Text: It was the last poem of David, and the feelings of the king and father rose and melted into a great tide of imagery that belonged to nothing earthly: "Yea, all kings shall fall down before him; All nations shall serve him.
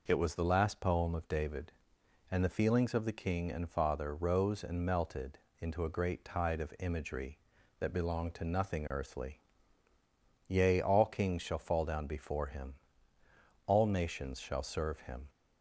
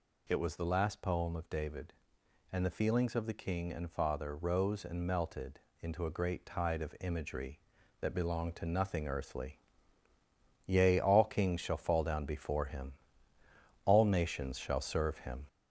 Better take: first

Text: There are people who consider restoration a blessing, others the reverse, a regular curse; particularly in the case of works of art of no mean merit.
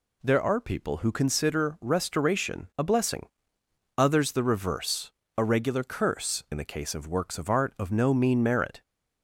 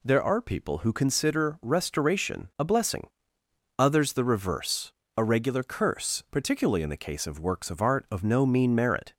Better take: second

